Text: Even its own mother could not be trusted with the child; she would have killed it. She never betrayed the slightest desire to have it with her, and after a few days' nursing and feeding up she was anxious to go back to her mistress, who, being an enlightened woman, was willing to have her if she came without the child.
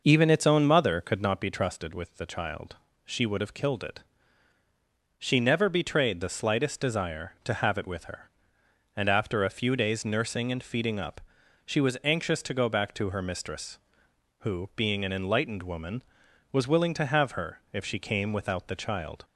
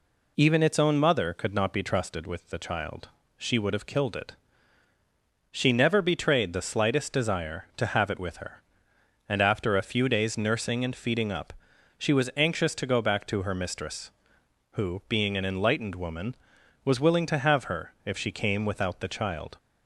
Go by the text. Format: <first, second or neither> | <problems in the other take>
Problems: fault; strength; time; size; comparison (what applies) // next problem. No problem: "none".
second | starts louder than the rest; noticeable; until 1.3 s; 5.5 dB // pauses between "up" and "she"; at 11.2 s; 0.44 s long; also in the second